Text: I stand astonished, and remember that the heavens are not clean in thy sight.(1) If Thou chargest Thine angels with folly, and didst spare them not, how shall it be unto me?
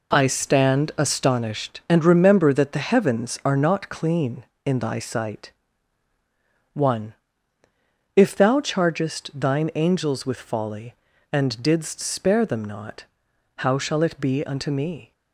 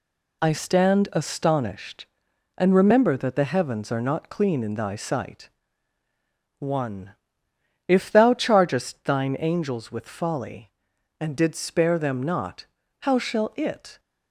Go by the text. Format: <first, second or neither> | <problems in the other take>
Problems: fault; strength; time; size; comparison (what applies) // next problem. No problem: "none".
first | stops before "be unto me"; at 13.9 s